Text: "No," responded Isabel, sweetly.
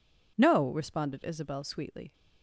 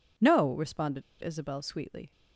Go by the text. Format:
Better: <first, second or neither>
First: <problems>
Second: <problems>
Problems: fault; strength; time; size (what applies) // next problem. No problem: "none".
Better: first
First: none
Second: pauses between "responded" and "Isabel"; slight; at 1.0 s; 0.18 s long